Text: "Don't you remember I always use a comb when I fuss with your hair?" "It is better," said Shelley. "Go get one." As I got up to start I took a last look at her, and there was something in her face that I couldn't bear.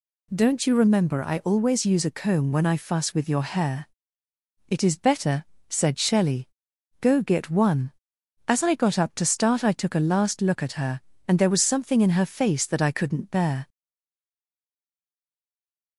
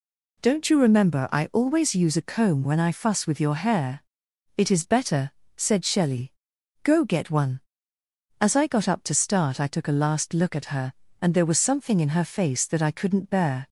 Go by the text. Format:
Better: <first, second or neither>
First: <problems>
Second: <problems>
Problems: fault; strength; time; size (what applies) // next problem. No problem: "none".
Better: second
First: stays silent after the last word; from 13.6 s on; 2.3 s long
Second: none